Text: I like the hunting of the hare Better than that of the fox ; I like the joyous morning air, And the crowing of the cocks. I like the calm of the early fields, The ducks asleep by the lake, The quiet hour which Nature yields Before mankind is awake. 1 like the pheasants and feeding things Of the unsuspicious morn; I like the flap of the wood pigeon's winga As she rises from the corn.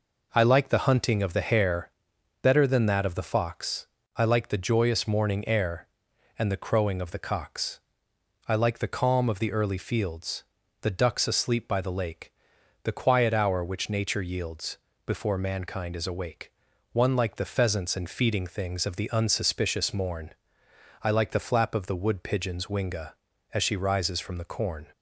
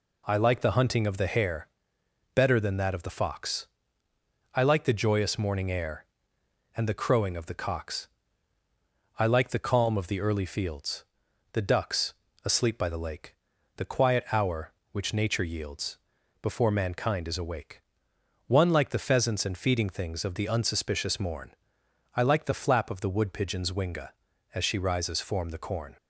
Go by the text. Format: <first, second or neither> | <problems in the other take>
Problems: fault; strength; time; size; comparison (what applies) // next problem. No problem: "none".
first | pauses between "hare" and "Better"; noticeable; at 1.6 s; 0.66 s long; noticeable in the first // pauses between "ducks" and "asleep"; slight; at 12.1 s; 0.28 s long // pauses between "yields" and "Before"; at 15.9 s; 0.42 s long; slight in the first // says "form" for "from"; at 25.2 s